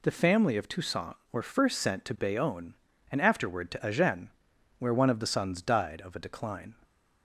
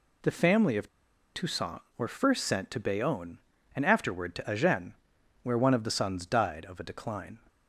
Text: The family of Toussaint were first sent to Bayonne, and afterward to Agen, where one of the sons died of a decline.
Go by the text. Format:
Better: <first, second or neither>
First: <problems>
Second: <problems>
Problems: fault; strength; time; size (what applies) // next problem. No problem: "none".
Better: first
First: none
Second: pauses between "of" and "Toussaint"; at 0.8 s; 0.45 s long